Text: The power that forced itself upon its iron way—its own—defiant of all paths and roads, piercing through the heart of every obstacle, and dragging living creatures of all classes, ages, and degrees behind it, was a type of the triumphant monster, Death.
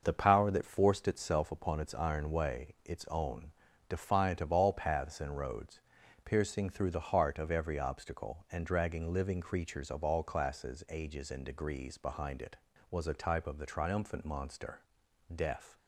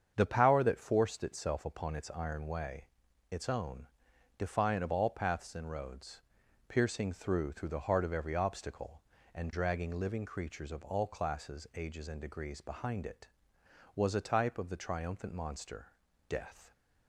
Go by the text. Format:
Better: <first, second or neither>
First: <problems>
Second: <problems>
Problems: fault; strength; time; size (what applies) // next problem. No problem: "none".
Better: first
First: starts louder than the rest; noticeable; until 1.0 s; 6 dB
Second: starts louder than the rest; strong; until 1.1 s; 7.5 dB // says "through" twice; at 7.5 s